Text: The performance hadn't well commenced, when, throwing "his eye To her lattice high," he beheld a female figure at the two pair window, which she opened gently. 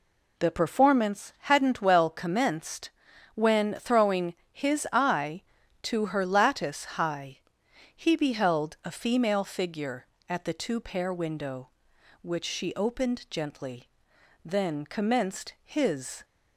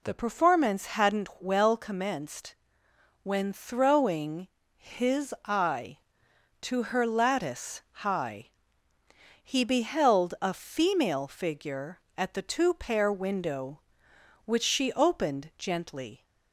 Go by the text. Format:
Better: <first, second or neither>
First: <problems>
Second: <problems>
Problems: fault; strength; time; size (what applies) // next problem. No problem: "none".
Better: second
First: pauses between "throwing" and "his"; slight; at 4.3 s; 0.18 s long // goes on to say "Then commenced his"; strong; from 14.4 s on; 1.8 s long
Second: pauses between "throwing" and "his"; slight; at 4.4 s; 0.28 s long